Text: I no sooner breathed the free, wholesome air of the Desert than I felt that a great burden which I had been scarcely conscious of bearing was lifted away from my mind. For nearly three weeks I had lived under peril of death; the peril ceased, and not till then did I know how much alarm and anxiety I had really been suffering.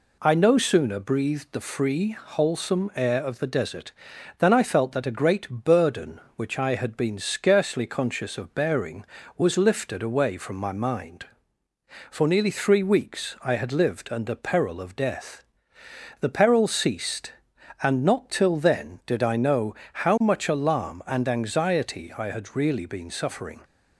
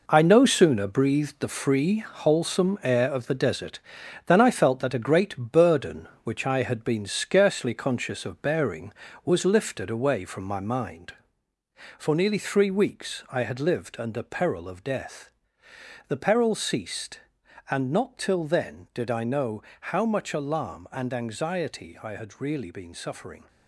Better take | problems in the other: first | gets quieter; strong; throughout; 8 dB // pauses between "know" and "how"; slight; at 19.6 s; 0.16 s long; slight in the first

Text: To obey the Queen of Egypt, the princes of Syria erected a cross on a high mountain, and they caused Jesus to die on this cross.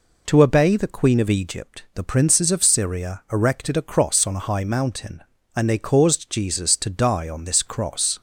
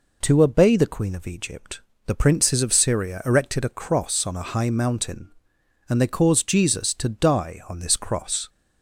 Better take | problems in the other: neither | none

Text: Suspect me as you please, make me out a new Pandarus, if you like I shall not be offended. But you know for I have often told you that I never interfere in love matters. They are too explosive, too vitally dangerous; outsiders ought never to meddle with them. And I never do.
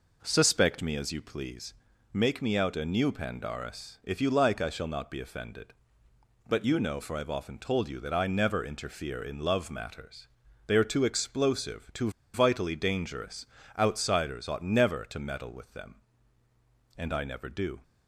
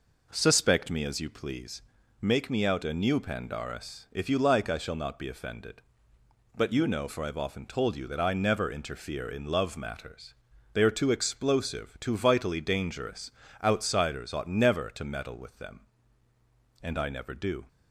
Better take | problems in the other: second | pauses between "too" and "vitally"; slight; at 12.1 s; 0.22 s long

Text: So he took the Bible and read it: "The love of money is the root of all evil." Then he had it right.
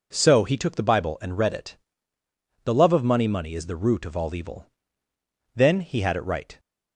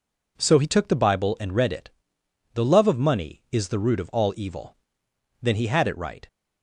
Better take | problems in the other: second | says "money" twice; at 3.2 s

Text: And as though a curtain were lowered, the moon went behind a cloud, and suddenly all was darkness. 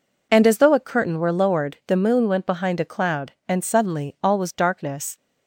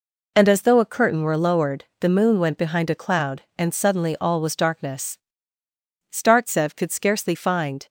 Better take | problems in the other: first | goes on to say "Startsev could scarcely find"; strong; from 6.1 s on; 1.7 s long

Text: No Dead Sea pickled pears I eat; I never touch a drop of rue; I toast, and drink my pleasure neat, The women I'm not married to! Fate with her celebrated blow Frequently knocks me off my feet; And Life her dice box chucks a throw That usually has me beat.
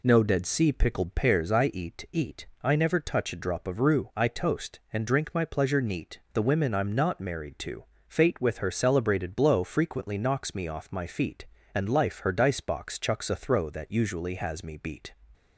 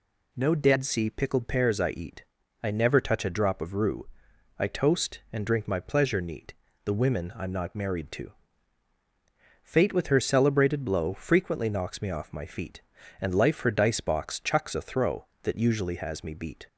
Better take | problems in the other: second | says "eat" twice; at 2.0 s

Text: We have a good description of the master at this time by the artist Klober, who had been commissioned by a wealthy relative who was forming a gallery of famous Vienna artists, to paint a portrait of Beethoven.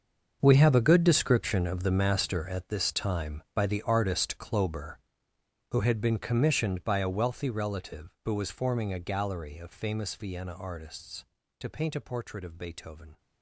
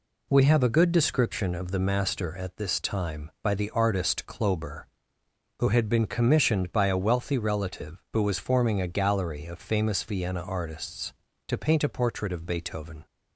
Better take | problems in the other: second | gets quieter; strong; throughout; 14.5 dB

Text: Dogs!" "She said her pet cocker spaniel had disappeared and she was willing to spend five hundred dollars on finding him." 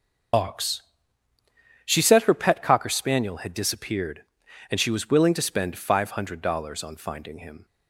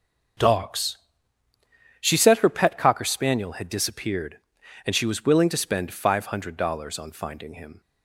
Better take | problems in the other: second | loses the start of "Dogs"; at 0.3 s; 105 ms // starts louder than the rest; noticeable; until 2.3 s; 6 dB; also in the second

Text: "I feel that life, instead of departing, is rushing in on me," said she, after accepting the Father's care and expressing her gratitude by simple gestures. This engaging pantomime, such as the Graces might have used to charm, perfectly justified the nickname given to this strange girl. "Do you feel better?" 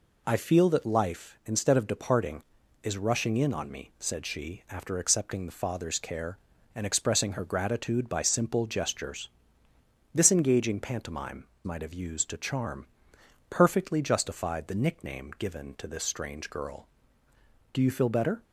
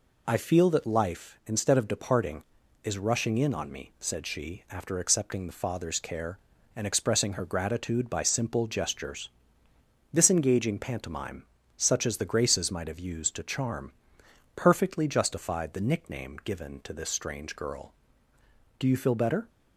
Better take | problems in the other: second | skips "such as the Graces"; at 11.5 s

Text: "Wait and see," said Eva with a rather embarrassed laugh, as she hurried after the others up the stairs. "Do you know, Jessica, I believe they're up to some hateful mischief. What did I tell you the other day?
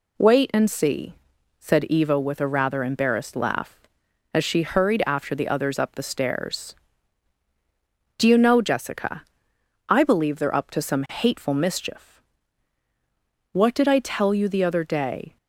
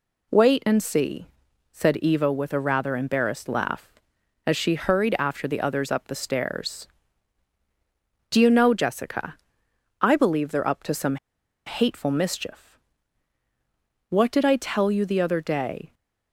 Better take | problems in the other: first | pauses between "some" and "hateful"; noticeable; at 11.1 s; 0.50 s long

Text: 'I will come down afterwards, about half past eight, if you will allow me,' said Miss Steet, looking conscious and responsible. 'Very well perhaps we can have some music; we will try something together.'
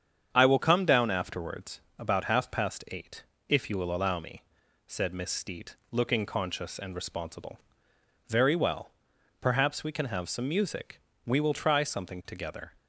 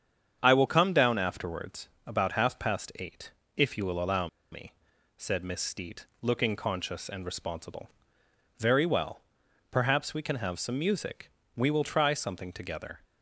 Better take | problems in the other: first | starts louder than the rest; strong; until 1.4 s; 8 dB; strong in the first // pauses between "allow" and "me"; slight; at 4.2 s; 0.23 s long // pauses between "well" and "perhaps"; noticeable; at 9.2 s; 0.50 s long; noticeable in the first

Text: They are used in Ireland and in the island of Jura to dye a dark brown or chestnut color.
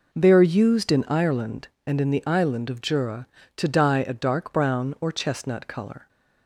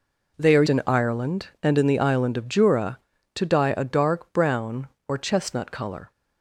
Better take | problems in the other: first | skips "used"; at 0.6 s

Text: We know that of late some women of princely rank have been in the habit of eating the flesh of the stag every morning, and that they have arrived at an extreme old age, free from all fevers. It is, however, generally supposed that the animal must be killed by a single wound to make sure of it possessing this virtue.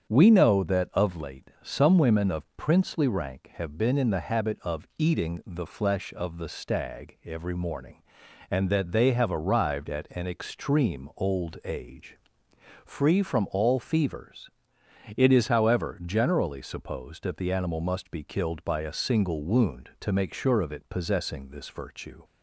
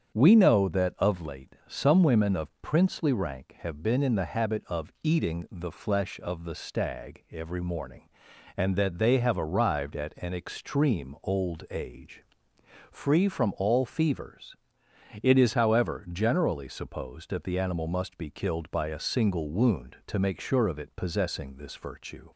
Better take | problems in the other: neither | starts louder than the rest; strong; the same in both

